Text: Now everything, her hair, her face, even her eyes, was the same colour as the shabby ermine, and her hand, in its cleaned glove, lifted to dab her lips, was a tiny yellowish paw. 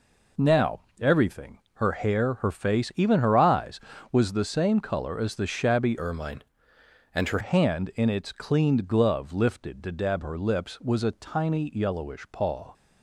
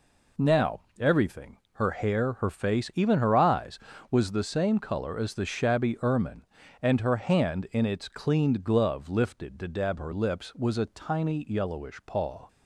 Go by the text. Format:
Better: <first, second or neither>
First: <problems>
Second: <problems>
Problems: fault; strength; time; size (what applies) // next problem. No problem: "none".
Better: second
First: pauses between "Now" and "everything"; slight; at 0.7 s; 0.20 s long // changes voice from "ermine" to "her"; from 5.9 to 7.3 s; 1.4 s long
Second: pauses between "Now" and "everything"; slight; at 0.7 s; 0.18 s long